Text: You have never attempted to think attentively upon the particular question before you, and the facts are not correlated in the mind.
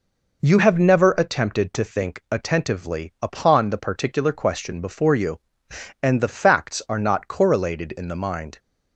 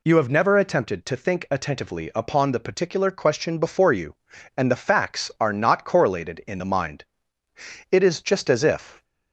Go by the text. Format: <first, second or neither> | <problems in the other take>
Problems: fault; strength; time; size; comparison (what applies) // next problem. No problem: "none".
first | goes on to say "It is just as if"; noticeable; from 7.9 s on; 1.1 s long